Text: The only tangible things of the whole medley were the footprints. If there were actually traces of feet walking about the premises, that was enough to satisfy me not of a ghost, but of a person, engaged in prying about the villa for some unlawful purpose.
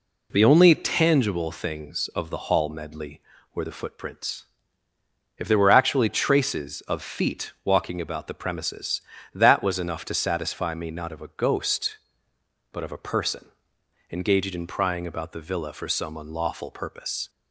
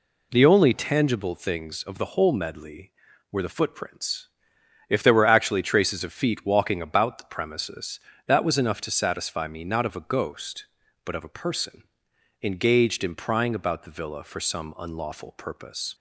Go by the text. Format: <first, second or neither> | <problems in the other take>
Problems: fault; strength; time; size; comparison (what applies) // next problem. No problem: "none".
second | says "hall" for "whole"; at 2.4 s